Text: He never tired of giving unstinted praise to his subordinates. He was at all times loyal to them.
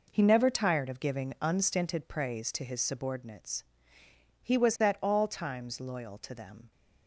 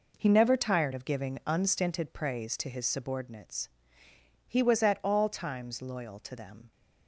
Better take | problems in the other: neither | none

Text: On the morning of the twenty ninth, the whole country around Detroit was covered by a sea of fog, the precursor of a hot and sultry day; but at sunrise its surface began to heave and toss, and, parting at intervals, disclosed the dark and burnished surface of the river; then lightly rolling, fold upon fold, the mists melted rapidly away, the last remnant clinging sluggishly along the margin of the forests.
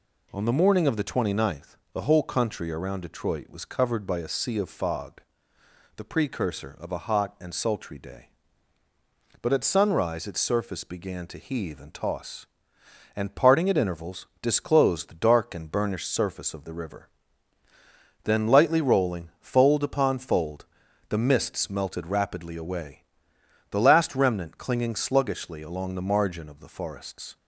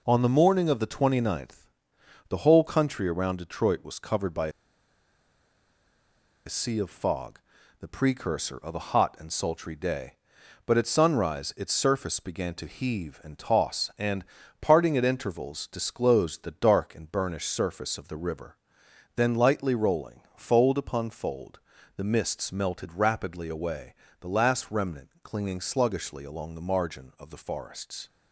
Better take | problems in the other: first | pauses between "by" and "a"; strong; at 4.4 s; 1.9 s long

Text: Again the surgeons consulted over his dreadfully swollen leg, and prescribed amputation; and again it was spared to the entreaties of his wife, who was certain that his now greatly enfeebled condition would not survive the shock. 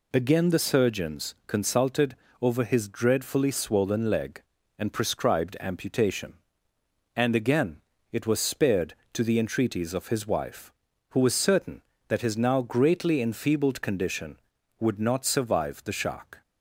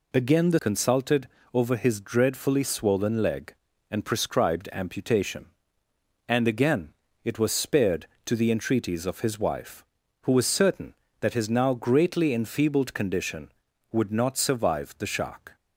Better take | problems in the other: first | skips "surgeons"; at 0.5 s // pauses between "consulted" and "over"; slight; at 1.2 s; 0.26 s long; slight in the first // pauses between "again" and "it"; slight; at 6.9 s; 0.32 s long; slight in the first

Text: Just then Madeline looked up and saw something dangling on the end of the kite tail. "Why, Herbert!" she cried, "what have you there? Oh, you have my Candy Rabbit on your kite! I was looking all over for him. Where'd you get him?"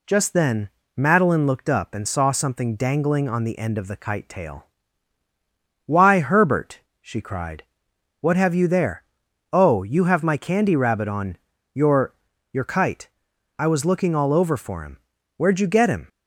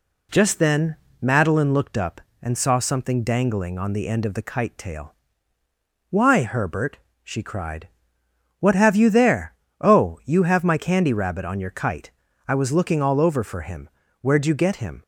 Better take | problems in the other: second | pauses between "then" and "Madeline"; slight; at 0.6 s; 0.28 s long; slight in the second // pauses between "on" and "your"; slight; at 11.3 s; 0.34 s long // says "your" twice; at 12.5 s

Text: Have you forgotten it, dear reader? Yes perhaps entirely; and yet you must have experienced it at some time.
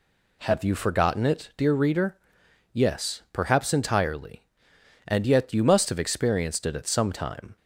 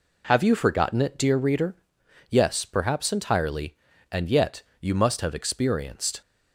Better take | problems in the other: first | pauses between "yet" and "you"; slight; at 4.6 s; 0.16 s long // stops before "it at some time"; at 6.2 s

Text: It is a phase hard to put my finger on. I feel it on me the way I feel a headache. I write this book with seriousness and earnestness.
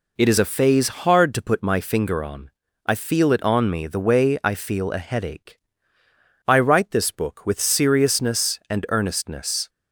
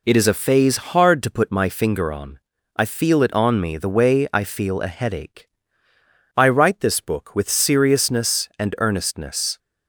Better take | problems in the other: neither | none

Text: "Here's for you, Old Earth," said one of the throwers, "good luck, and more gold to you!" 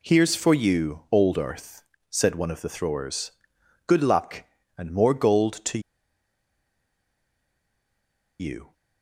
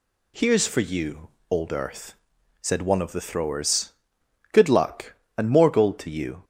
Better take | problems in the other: second | pauses between "to" and "you"; strong; at 5.7 s; 2.6 s long

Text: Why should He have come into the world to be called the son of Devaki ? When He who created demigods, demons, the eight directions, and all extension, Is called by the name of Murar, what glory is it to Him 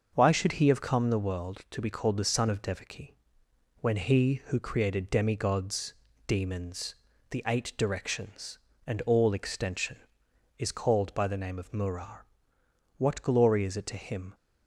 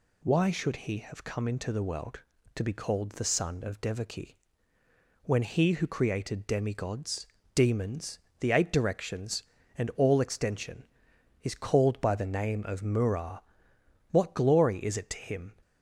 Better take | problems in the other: second | starts louder than the rest; noticeable; until 1.1 s; 6 dB // skips "into"; at 1.0 s

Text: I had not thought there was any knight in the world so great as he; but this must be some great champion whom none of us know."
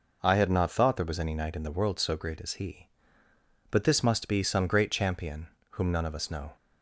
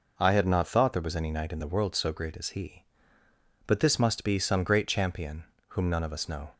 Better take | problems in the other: neither | pauses between "champion" and "whom"; slight; the same in both

